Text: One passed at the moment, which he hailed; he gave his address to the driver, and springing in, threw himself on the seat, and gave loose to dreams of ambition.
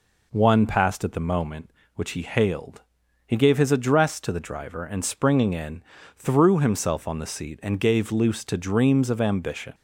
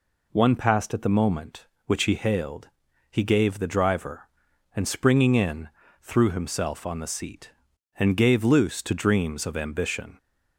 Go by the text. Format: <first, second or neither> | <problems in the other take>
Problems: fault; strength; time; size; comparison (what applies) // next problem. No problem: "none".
first | skips "his address to"; at 3.5 s